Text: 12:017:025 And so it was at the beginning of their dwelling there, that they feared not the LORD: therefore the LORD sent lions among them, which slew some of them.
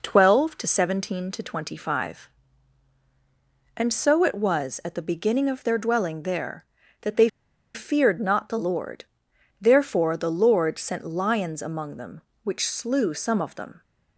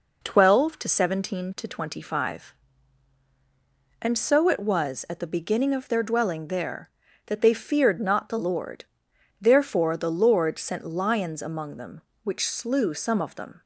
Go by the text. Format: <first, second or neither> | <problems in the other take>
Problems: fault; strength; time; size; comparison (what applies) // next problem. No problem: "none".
second | pauses between "they" and "feared"; noticeable; at 7.2 s; 0.46 s long